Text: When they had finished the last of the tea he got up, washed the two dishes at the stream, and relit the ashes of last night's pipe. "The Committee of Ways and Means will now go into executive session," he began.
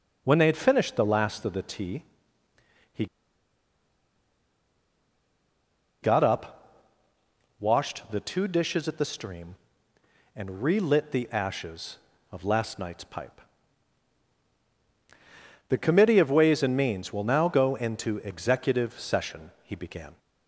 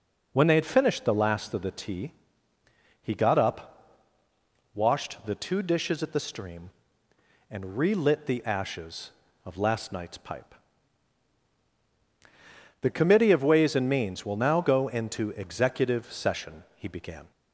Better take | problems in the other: second | pauses between "tea" and "he"; noticeable; at 2.0 s; 0.94 s long; noticeable in the second // pauses between "he" and "got"; strong; at 3.0 s; 2.9 s long

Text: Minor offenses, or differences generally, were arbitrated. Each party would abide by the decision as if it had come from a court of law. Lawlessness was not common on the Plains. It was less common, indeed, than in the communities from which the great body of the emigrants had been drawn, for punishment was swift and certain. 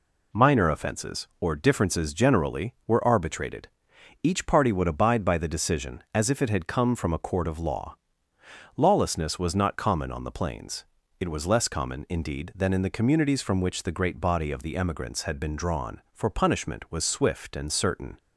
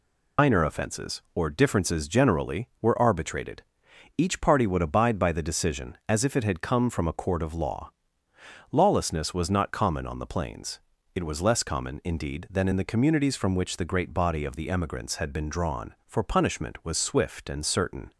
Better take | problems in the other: first | loses the start of "Minor"; at 0.3 s; 110 ms

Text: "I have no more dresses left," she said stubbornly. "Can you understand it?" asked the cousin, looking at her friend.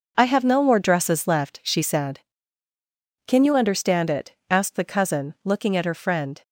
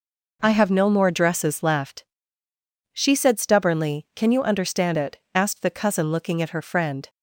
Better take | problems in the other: second | skips "stubbornly"; at 2.7 s

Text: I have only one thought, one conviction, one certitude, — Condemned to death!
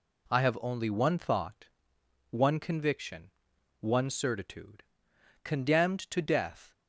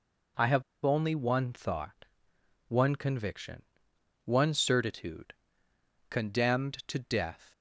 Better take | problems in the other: first | pauses between "have" and "only"; slight; at 0.6 s; 0.22 s long

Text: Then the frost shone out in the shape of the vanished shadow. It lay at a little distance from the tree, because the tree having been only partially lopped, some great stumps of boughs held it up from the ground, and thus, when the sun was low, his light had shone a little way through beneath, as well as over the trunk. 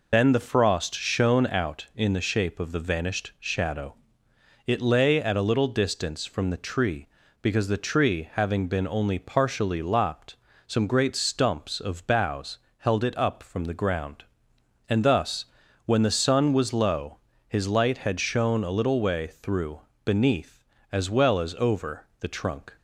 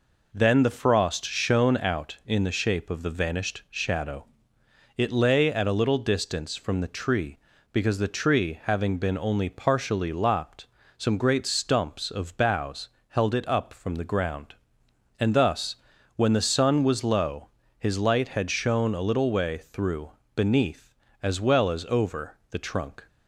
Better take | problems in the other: second | loses the start of "Then"; at 0.1 s; 100 ms // pauses between "boughs" and "held"; slight; at 12.5 s; 0.20 s long; slight in the second // pauses between "through" and "beneath"; slight; at 19.8 s; 0.24 s long; slight in the second

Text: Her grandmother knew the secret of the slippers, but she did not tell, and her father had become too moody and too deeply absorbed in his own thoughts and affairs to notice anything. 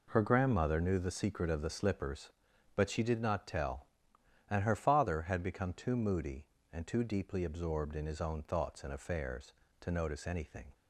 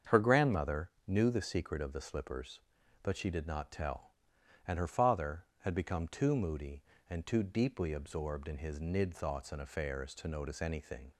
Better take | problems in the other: first | starts louder than the rest; strong; until 1.2 s; 7.5 dB // pauses between "grandmother" and "knew"; slight; at 0.8 s; 0.18 s long // says "nid" for "own"; at 8.7 s

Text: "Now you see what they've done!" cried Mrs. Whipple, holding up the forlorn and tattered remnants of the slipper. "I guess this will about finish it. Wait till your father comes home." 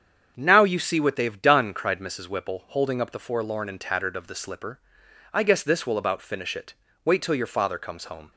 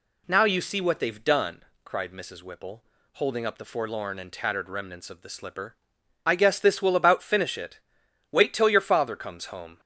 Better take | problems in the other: second | starts louder than the rest; strong; until 1.3 s; 7.5 dB // skips "remnants"; at 4.1 s

